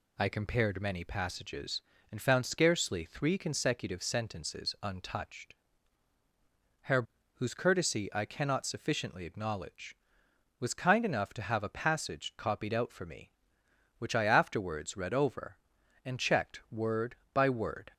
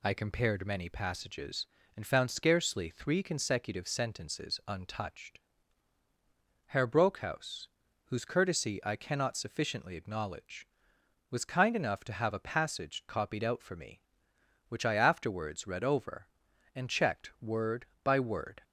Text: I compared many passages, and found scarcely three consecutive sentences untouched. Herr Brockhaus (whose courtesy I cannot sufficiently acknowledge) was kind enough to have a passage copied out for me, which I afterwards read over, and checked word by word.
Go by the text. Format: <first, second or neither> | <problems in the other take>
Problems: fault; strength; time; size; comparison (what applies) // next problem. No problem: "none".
second | skips "Brockhaus"; at 7.1 s